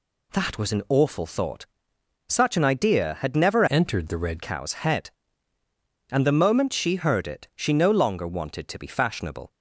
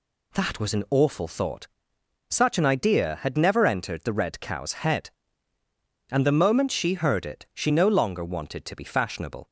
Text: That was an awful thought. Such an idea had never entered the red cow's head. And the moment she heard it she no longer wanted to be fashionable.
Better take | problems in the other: second | changes voice from "entered" to "red"; from 3.6 to 4.4 s; 0.8 s long

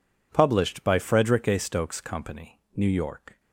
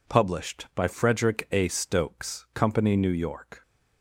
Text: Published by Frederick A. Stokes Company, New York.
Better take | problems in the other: neither | none

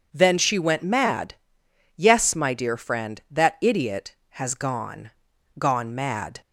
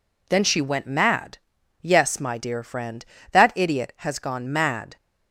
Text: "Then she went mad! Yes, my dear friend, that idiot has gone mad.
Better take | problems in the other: second | says "gone" twice; at 5.5 s

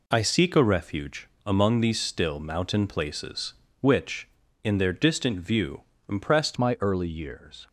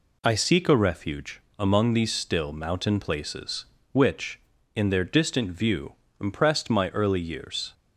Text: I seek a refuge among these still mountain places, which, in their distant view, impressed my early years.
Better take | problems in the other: second | pauses between "refuge" and "among"; slight; at 1.2 s; 0.22 s long; slight in the second // changes voice at "my"; from 6.5 s on; 1.1 s long

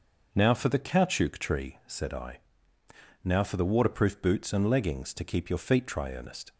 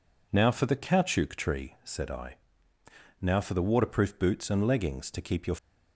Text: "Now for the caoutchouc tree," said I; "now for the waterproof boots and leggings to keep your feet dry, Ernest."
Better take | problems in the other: first | stops before "feet dry Ernest"; at 5.5 s

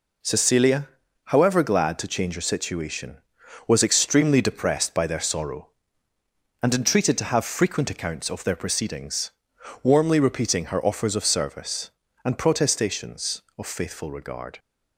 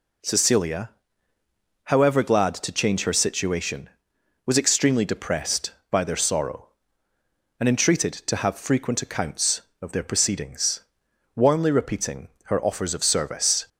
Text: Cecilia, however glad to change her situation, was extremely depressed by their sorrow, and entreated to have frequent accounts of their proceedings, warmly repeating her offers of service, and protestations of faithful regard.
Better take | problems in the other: first | pauses between "repeating" and "her"; slight; at 12.2 s; 0.18 s long // stops before "and protestations of faithful regard"; at 13.6 s

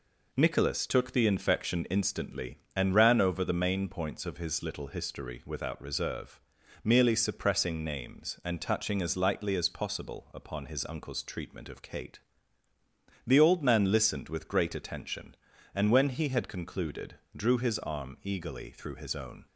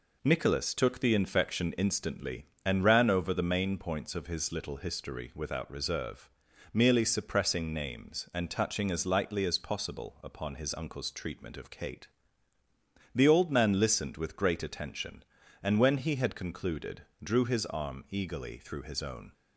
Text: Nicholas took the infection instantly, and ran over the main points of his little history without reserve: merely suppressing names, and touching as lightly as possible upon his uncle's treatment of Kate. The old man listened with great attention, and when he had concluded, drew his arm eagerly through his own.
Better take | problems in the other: neither | none

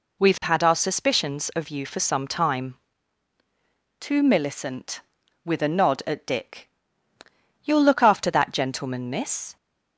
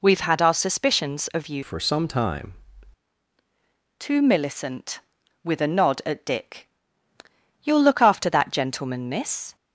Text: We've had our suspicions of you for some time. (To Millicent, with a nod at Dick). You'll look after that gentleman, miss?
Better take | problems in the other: first | changes voice from "for" to "time"; from 1.6 to 2.5 s; 0.9 s long

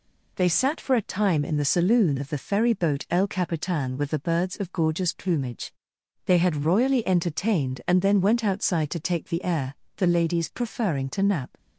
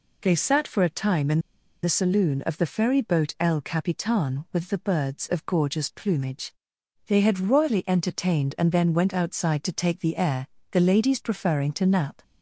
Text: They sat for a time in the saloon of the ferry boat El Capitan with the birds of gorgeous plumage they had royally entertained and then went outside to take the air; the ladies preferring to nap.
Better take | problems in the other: first | pauses between "in" and "the"; at 1.3 s; 0.44 s long // pauses between "plumage" and "they"; noticeable; at 6.5 s; 0.54 s long; noticeable in the first

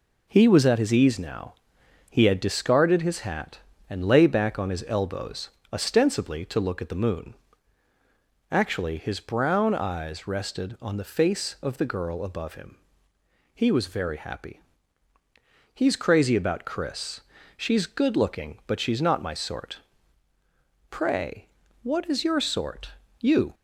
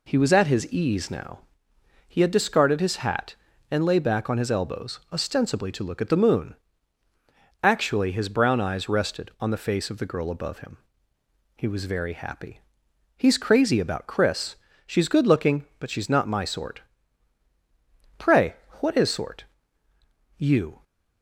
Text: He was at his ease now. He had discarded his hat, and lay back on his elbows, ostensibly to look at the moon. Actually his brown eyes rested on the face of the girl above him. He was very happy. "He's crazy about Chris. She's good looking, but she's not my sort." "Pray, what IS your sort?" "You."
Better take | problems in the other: first | skips "your"; at 19.1 s

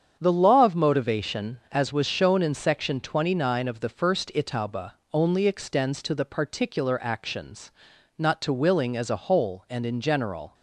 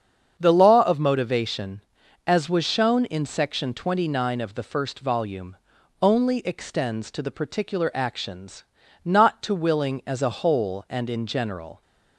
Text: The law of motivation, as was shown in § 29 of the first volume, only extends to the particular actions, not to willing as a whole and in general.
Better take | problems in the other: second | starts louder than the rest; strong; until 1.2 s; 8 dB; strong in the second // says "itauba" for "volume"; at 4.3 s

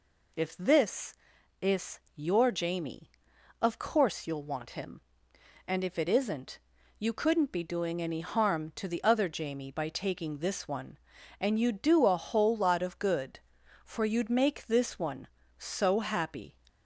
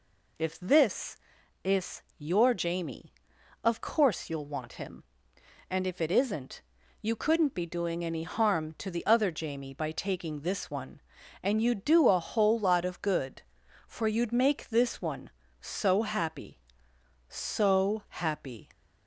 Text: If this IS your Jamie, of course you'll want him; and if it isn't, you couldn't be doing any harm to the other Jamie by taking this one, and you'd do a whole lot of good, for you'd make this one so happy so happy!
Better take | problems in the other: second | pauses between "IS" and "your"; slight; at 1.9 s; 0.16 s long; slight in the second // stops before "so happy"; at 16.6 s

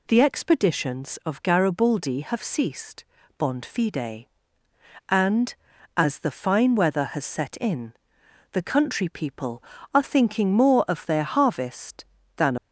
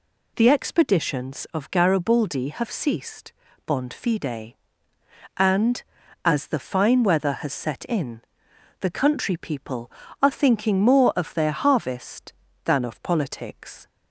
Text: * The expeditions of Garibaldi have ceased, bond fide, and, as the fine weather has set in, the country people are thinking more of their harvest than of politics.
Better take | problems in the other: second | stops before "of politics"; at 12.5 s

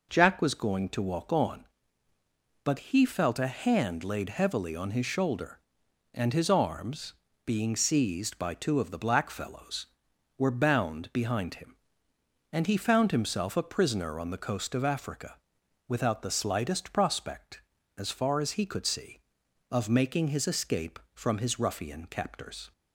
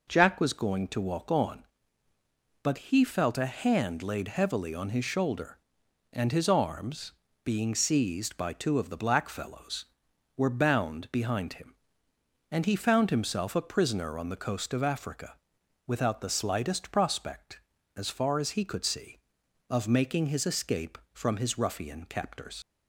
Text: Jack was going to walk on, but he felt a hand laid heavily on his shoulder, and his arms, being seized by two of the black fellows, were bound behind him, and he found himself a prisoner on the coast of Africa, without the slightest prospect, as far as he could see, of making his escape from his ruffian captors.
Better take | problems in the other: first | leaves "captors" unfinished; at 22.6 s; 85 ms

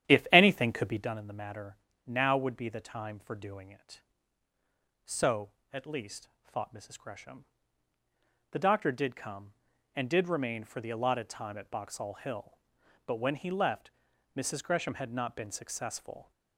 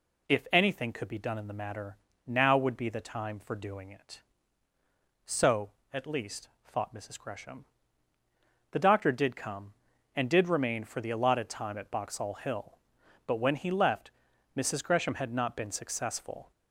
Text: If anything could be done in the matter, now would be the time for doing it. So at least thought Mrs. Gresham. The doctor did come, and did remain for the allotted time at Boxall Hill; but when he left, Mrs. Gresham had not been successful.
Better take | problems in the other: second | starts louder than the rest; strong; until 1.1 s; 10.5 dB // pauses between "least" and "thought"; slight; at 6.2 s; 0.16 s long; slight in the second

